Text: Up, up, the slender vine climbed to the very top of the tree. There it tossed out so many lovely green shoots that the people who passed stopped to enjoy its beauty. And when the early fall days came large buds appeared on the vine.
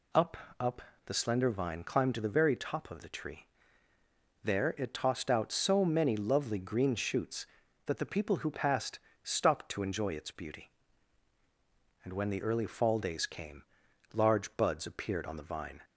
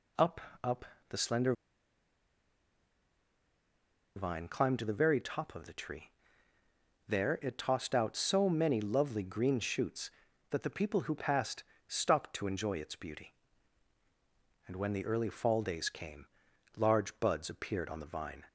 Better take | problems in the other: first | pauses between "slender" and "vine"; strong; at 1.5 s; 2.6 s long // pauses between "passed" and "stopped"; slight; at 11.6 s; 0.24 s long; slight in the first // pauses between "came" and "large"; noticeable; at 16.2 s; 0.52 s long; noticeable in the first

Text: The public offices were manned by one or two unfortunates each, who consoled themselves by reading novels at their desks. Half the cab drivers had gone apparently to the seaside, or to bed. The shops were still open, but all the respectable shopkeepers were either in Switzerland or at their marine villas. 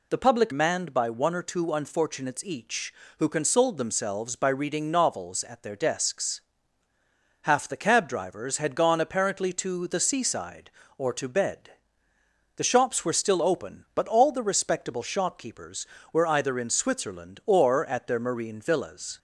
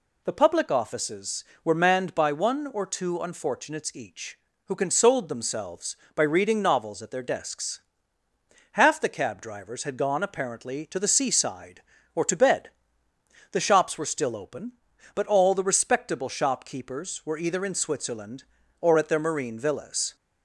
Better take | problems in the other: second | skips "offices were"; at 0.5 s

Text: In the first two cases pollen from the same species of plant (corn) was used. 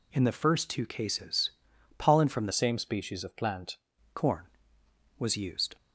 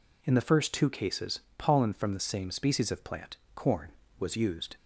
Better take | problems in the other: second | pauses between "cases" and "pollen"; noticeable; at 1.4 s; 0.48 s long; slight in the second // changes voice from "same" to "plant"; from 2.5 to 3.7 s; 1.2 s long

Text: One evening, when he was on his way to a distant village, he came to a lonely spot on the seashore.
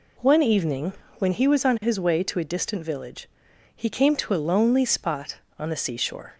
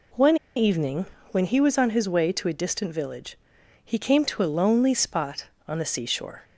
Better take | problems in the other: first | pauses between "One" and "evening"; slight; at 0.3 s; 0.21 s long

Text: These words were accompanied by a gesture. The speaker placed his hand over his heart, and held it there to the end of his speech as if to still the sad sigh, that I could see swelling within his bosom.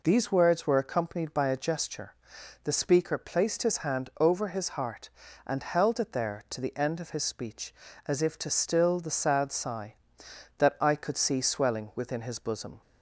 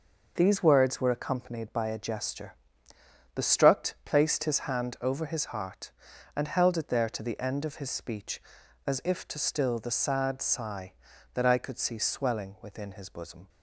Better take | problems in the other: first | says "struct" for "speaker"; at 3.4 s

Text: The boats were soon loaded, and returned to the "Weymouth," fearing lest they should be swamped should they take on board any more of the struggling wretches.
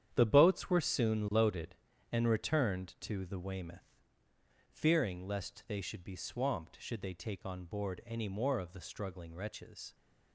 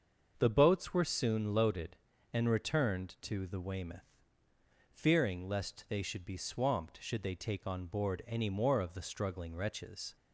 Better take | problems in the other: second | gets quieter; strong; throughout; 10 dB // starts louder than the rest; strong; until 1.1 s; 9.5 dB; also in the second

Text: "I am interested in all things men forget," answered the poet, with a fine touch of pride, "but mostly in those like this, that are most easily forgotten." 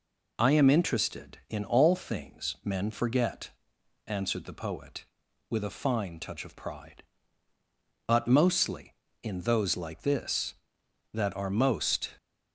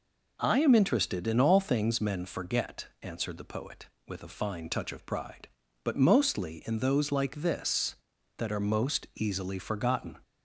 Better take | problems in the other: second | stops before "easily forgotten"; at 12.1 s

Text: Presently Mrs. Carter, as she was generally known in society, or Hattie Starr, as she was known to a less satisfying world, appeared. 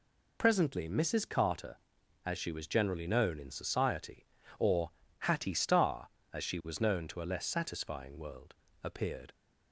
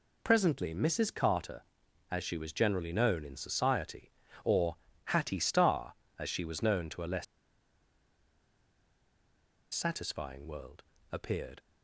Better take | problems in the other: first | pauses between "or" and "Hattie"; slight; at 4.7 s; 0.30 s long; slight in the first // pauses between "less" and "satisfying"; strong; at 7.2 s; 2.4 s long

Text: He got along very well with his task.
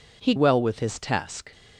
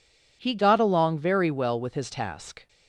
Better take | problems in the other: second | skips "got along very"; at 0.3 s

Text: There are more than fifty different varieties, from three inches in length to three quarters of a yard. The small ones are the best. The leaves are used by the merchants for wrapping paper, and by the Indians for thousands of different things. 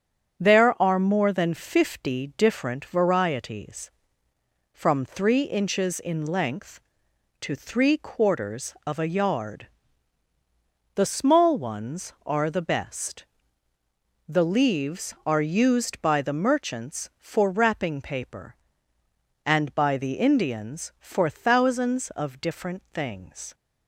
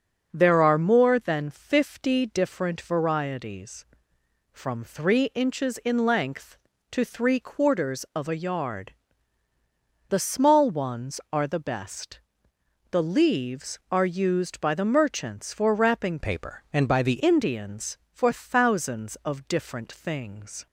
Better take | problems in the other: first | starts louder than the rest; noticeable; until 1.3 s; 6 dB; strong in the first // changes voice from "paper" to "the"; from 16.2 to 17.2 s; 1.0 s long

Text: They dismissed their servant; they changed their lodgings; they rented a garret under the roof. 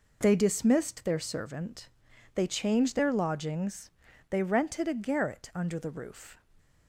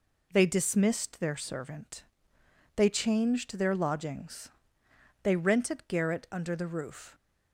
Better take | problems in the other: first | skips "a"; at 5.8 s

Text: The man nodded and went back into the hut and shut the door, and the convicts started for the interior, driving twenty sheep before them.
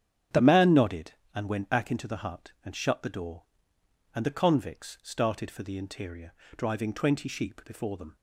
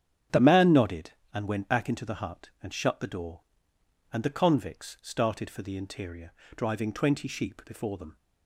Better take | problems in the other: neither | starts louder than the rest; strong; the same in both

